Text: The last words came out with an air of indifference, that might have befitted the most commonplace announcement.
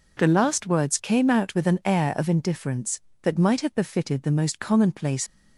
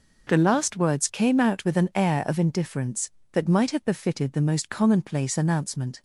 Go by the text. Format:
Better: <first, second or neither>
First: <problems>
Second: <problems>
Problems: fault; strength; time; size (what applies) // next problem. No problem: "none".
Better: second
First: stops before "announcement"; at 5.2 s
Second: none